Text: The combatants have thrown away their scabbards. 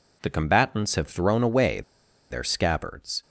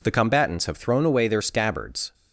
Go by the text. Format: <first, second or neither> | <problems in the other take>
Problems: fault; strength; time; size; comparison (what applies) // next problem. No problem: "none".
second | pauses between "away" and "their"; noticeable; at 1.8 s; 0.49 s long